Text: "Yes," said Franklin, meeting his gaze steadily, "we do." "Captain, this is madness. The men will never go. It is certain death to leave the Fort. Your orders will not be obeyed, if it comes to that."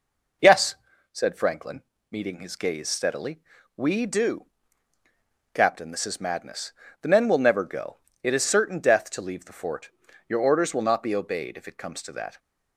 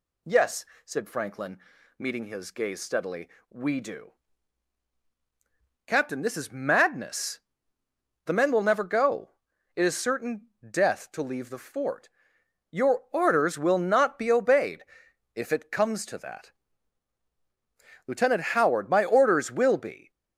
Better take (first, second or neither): first